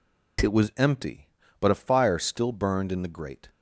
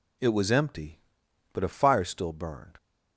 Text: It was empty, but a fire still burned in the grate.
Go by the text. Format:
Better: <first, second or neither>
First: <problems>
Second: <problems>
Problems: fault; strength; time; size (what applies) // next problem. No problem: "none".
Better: first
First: none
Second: stops before "in the grate"; at 2.7 s